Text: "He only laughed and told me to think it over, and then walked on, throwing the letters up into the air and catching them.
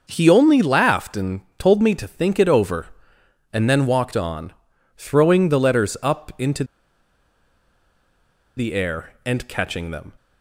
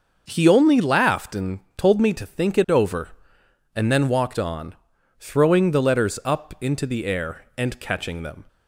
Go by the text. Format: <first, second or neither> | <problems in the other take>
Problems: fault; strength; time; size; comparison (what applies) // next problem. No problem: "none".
second | starts louder than the rest; noticeable; until 1.0 s; 6 dB; also in the second // pauses between "and" and "told"; slight; at 1.4 s; 0.16 s long; slight in the second // pauses between "into" and "the"; strong; at 6.6 s; 1.9 s long